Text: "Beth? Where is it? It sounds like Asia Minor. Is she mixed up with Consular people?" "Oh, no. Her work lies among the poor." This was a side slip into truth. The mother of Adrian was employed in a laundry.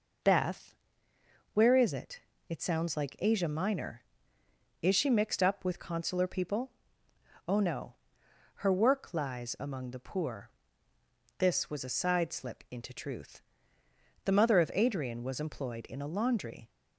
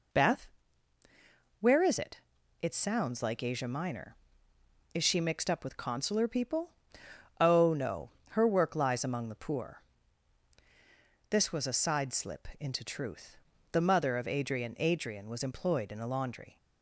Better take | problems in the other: first | says "Adrian" twice; at 14.7 s

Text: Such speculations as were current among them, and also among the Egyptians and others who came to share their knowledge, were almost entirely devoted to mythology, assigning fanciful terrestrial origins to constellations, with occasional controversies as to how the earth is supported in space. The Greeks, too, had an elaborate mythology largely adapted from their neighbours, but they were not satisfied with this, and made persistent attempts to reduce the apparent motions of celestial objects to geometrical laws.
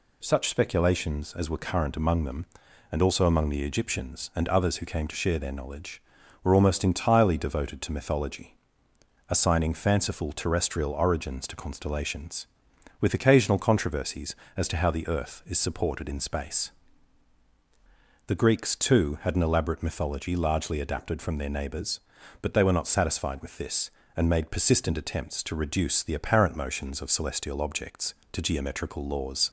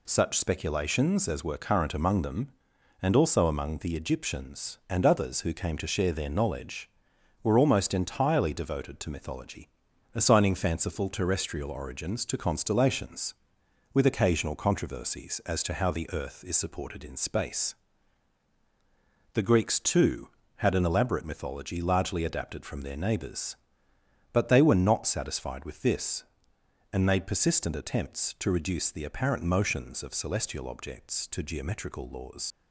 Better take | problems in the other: first | leaves "laws" unfinished; at 32.5 s; 60 ms

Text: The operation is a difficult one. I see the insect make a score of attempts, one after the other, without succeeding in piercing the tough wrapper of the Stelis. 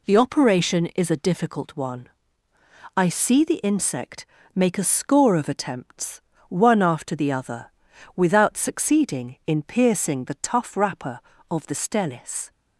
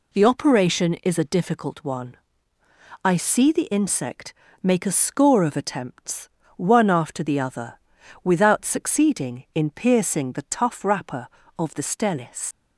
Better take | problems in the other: first | pauses between "insect" and "make"; slight; at 4.3 s; 0.28 s long; slight in the first // leaves "Stelis" unfinished; at 12.5 s; 65 ms

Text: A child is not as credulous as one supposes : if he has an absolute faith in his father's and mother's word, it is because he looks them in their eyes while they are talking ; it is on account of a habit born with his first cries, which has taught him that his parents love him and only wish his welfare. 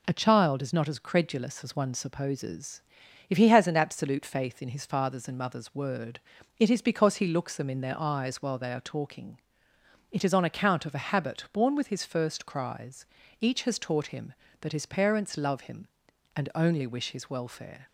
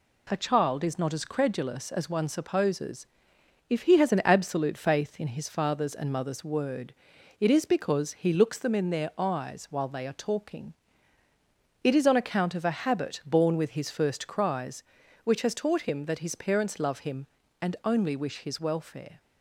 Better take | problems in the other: second | says "each" for "which"; at 13.4 s

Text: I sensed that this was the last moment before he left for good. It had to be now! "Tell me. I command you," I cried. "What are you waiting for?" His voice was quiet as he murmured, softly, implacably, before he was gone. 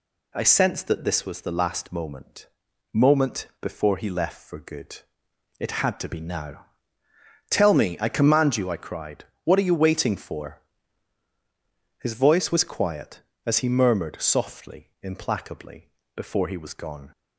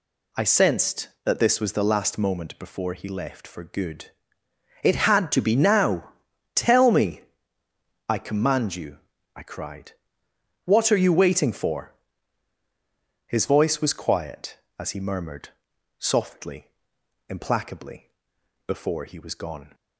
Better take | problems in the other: second | says "moment" twice; at 2.9 s

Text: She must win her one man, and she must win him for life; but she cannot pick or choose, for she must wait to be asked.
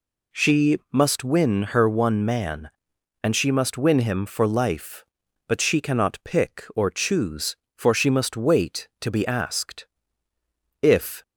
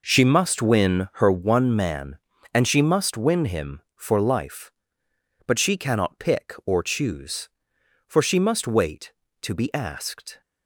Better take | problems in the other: second | goes on to say "If"; slight; from 10.8 s on; 0.42 s long

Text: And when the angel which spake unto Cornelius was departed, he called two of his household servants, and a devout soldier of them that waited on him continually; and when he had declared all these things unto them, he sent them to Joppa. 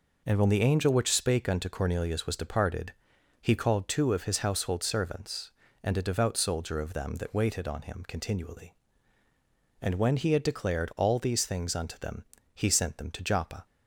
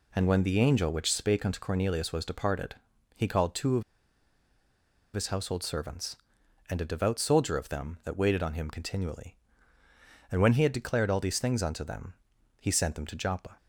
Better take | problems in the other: first | pauses between "of" and "his"; strong; at 3.8 s; 1.3 s long

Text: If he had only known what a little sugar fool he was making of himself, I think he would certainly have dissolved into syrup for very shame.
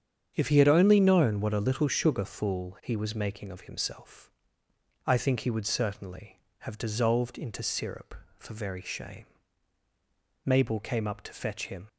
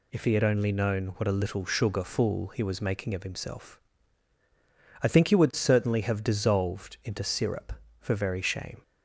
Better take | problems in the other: second | starts louder than the rest; strong; until 1.3 s; 8 dB // goes on to say "Mabel came up to fetch him"; from 10.4 s on; 1.4 s long

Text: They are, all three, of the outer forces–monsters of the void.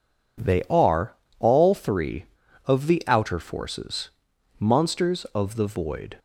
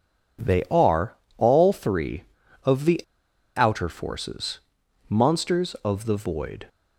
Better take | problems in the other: first | pauses between "the" and "outer"; noticeable; at 3.0 s; 0.54 s long

